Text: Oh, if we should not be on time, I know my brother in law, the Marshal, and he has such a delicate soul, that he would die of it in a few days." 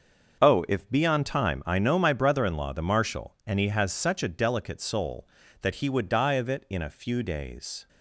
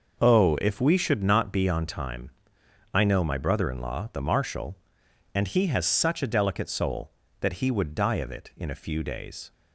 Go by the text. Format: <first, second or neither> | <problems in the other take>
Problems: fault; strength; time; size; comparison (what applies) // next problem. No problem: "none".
second | starts louder than the rest; until 1.4 s; 6.5 dB // skips "we should not"; at 0.8 s